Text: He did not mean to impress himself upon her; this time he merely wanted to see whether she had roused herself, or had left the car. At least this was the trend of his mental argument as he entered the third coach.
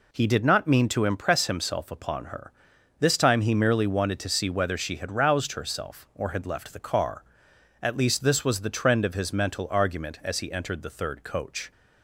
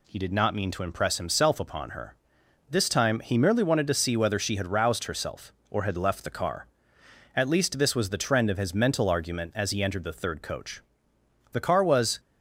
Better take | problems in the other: first | goes on to say "The car was"; noticeable; from 11.5 s on; 0.68 s long

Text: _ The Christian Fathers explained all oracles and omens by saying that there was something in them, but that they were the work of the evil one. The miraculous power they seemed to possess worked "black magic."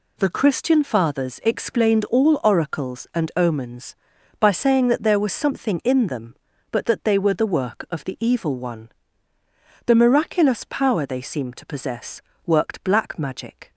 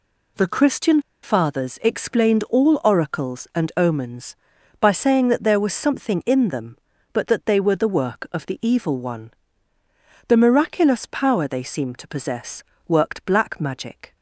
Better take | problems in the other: first | pauses between "Christian" and "Fathers"; slight; at 1.0 s; 0.22 s long // pauses between "possess" and "worked"; slight; at 12.6 s; 0.24 s long; slight in the first

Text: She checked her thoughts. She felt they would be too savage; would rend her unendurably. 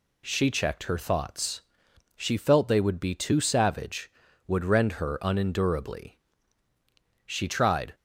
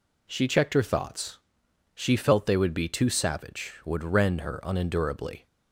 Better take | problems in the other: second | goes on to say "She tried"; noticeable; from 7.2 s on; 0.70 s long

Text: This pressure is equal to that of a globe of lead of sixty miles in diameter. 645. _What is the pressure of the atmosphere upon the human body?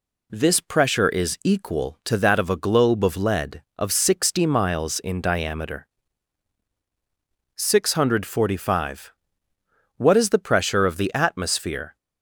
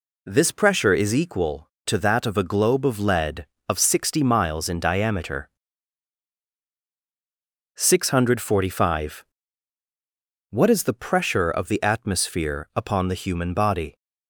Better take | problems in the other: second | stops before "upon the human body"; at 11.9 s

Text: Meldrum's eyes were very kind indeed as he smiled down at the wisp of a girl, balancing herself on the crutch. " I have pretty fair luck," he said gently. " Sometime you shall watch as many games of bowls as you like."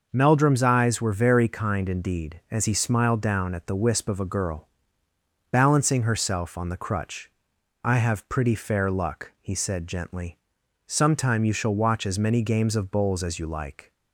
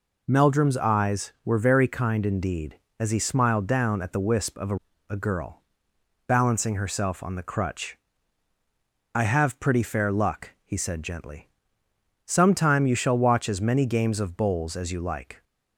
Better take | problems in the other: first | says "a" twice; at 5.0 s

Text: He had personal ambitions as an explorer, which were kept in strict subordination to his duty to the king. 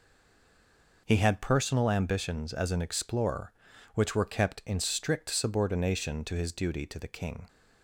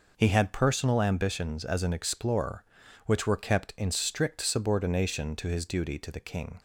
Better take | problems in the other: second | stays silent before the first word; until 1.0 s; 1.0 s long

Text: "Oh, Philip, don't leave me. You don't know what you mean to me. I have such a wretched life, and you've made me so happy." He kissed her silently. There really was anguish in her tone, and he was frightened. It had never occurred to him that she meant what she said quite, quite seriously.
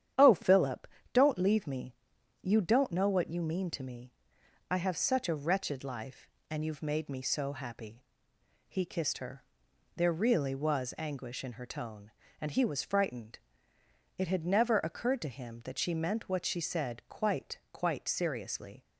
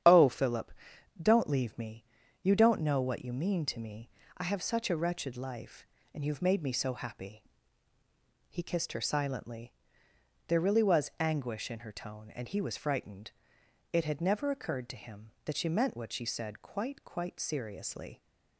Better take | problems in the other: second | starts louder than the rest; strong; until 1.4 s; 9.5 dB; strong in the second // skips "silently"; at 9.6 s

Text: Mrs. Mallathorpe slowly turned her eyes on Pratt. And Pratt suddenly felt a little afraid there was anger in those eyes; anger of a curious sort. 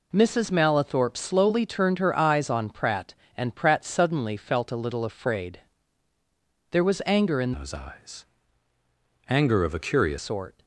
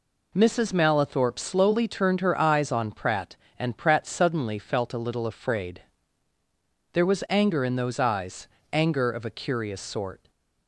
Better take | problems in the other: second | pauses between "afraid" and "there"; at 5.5 s; 1.1 s long; also in the second // changes voice from "those" to "curious"; from 7.5 to 10.1 s; 2.6 s long

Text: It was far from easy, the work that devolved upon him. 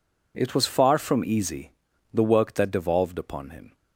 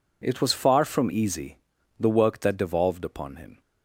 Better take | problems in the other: neither | none

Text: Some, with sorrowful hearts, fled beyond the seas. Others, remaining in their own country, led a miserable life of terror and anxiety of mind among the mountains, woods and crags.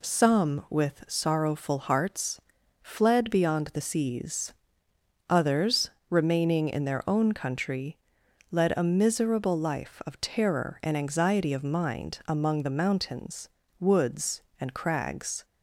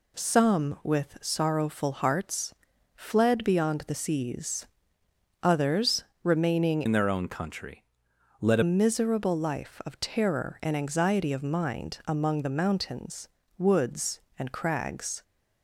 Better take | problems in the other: first | changes voice from "in" to "a"; from 6.8 to 8.6 s; 1.8 s long

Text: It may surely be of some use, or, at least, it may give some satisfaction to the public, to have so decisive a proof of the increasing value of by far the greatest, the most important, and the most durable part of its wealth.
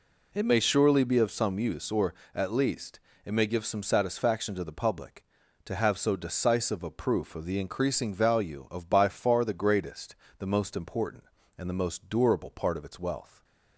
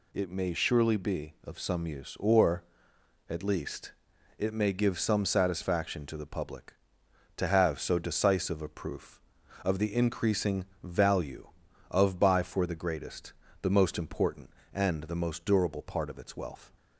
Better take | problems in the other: first | pauses between "increasing" and "value"; slight; at 10.6 s; 0.18 s long // says "for" for "far"; at 12.4 s

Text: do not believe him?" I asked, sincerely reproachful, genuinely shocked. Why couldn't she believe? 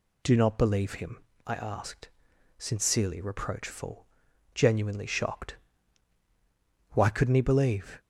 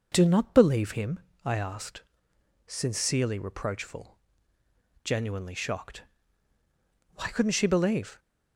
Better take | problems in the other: second | says "he" for "she"; at 7.3 s

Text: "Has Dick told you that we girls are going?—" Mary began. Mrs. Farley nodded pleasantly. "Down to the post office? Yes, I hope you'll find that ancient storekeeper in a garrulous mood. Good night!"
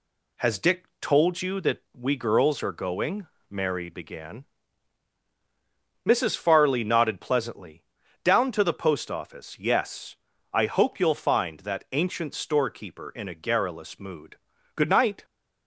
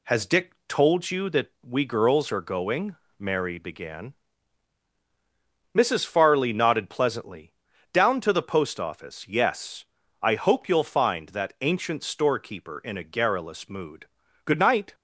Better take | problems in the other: neither | none

